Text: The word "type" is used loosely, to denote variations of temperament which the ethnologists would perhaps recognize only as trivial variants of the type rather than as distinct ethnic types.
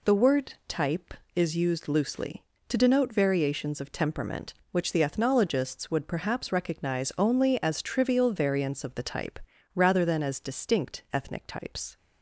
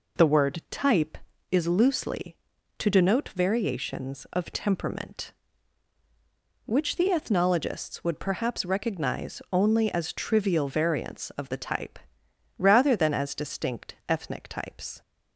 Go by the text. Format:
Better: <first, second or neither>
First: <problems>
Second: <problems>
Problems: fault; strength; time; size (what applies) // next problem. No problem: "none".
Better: first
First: pauses between "type" and "rather"; at 9.3 s; 0.38 s long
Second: skips "used"; at 1.6 s // pauses between "type" and "rather"; noticeable; at 11.9 s; 0.62 s long